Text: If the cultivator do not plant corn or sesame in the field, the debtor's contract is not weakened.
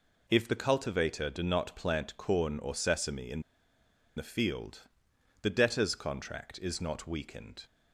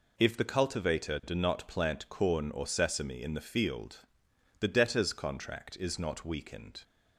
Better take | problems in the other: second | pauses between "in" and "the"; noticeable; at 3.4 s; 0.74 s long

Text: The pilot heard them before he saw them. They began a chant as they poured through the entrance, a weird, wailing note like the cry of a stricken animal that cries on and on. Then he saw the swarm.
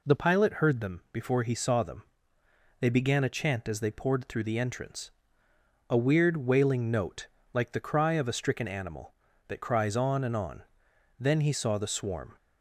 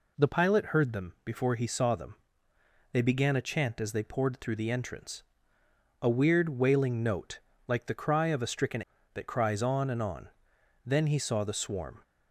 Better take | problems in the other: first | pauses between "note" and "like"; slight; at 7.3 s; 0.28 s long; slight in the first // skips "animal"; at 8.9 s

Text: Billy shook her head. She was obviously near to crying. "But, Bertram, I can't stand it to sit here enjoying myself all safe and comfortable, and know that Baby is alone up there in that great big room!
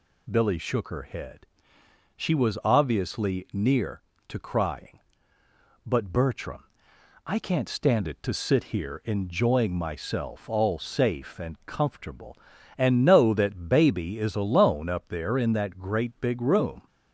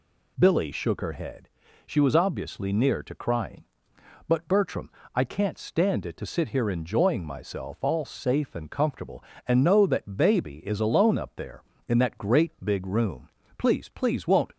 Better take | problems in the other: first | goes on to say "Please please won't"; noticeable; from 13.5 s on; 0.94 s long

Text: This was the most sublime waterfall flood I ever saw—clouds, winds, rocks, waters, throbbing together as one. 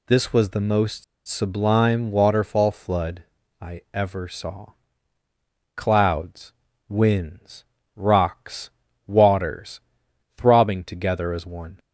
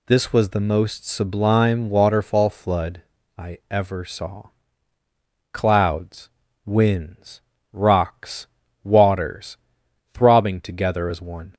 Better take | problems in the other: second | pauses between "most" and "sublime"; slight; at 1.0 s; 0.24 s long // pauses between "flood" and "I"; slight; at 3.2 s; 0.36 s long; slight in the second

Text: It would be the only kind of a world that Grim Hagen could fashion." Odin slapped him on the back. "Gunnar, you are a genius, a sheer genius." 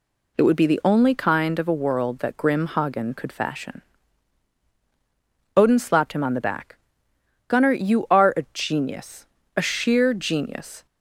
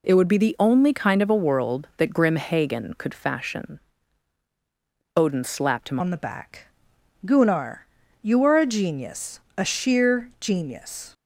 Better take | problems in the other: first | changes voice at "on"; from 6.0 s on; 5.1 s long

